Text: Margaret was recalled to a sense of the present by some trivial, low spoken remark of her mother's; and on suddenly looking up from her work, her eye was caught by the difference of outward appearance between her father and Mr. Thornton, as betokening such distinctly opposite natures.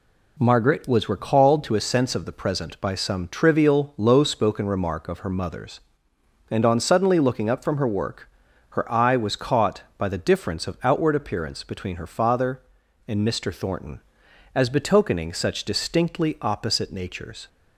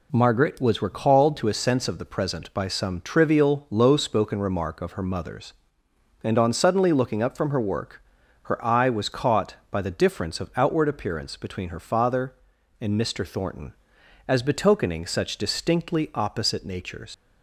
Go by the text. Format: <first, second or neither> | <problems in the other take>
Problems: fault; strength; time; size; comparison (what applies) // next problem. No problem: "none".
first | leaves "natures" unfinished; at 17.1 s; 65 ms